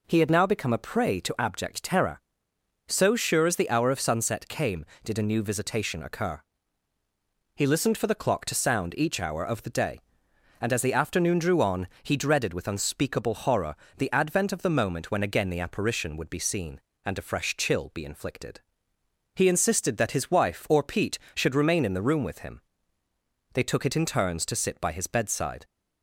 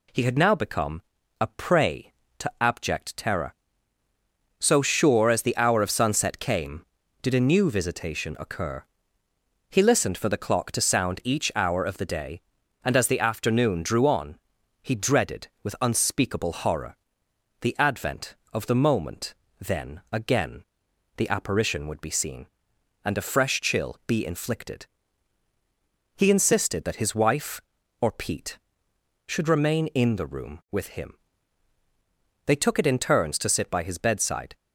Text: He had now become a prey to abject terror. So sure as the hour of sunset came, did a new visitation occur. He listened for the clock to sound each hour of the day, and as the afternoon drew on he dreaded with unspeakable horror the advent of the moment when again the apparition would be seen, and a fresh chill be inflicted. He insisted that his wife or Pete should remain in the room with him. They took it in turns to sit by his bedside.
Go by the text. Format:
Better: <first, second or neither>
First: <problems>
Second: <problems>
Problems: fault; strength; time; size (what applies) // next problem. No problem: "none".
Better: first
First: pauses between "on" and "he"; slight; at 11.8 s; 0.16 s long // pauses between "horror" and "the"; slight; at 13.7 s; 0.22 s long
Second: pauses between "become" and "a"; at 1.0 s; 0.38 s long // pauses between "on" and "he"; noticeable; at 14.3 s; 0.46 s long // pauses between "horror" and "the"; noticeable; at 16.9 s; 0.66 s long // says "then" for "when"; at 19.6 s // pauses between "again" and "the"; noticeable; at 20.6 s; 0.54 s long